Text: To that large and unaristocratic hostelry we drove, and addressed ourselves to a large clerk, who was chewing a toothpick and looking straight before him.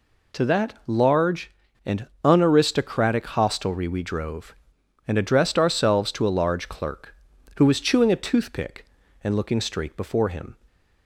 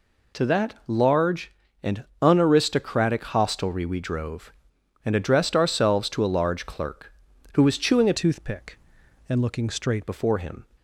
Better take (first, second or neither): first